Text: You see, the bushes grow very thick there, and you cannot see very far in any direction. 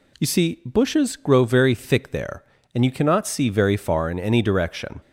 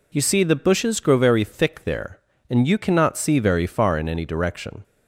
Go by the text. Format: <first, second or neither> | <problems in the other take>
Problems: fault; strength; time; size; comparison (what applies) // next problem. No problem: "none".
second | skips "the"; at 0.6 s